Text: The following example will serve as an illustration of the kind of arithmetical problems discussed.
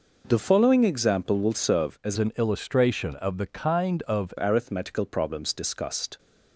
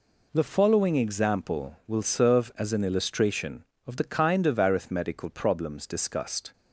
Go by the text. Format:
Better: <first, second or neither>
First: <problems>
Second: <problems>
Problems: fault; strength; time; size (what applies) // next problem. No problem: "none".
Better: second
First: changes voice from "an" to "of"; from 2.1 to 4.3 s; 2.2 s long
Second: none